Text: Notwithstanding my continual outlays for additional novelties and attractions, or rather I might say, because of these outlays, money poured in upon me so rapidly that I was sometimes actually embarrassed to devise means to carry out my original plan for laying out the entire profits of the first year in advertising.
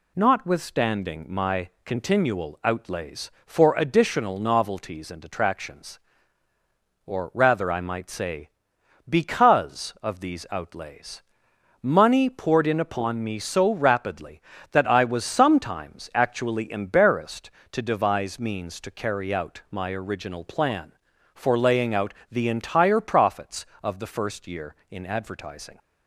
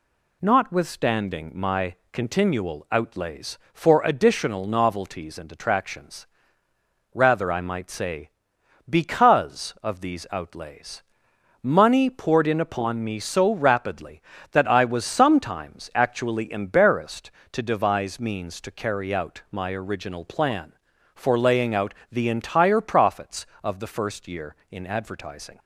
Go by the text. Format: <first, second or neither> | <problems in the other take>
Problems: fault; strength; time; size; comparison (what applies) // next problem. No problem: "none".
first | pauses between "my" and "continual"; slight; at 1.9 s; 0.18 s long; slight in the first // skips "or"; at 6.6 s // pauses between "out" and "the"; slight; at 21.9 s; 0.18 s long; slight in the first